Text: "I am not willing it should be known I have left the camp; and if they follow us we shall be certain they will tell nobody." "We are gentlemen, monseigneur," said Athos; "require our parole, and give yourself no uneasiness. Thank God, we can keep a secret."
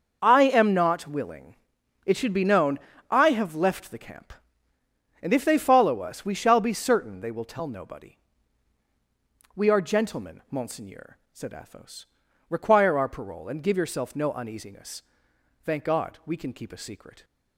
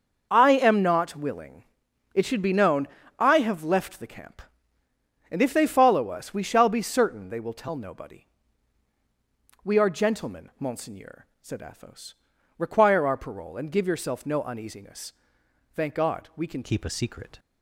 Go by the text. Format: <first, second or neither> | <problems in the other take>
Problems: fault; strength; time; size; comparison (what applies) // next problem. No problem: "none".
first | starts louder than the rest; until 1.3 s; 6 dB; also in the first // pauses between "willing" and "it"; noticeable; at 1.6 s; 0.50 s long; noticeable in the first // pauses between "known" and "I"; slight; at 2.8 s; 0.32 s long; slight in the first // changes voice at "keep"; from 16.6 s on; 0.7 s long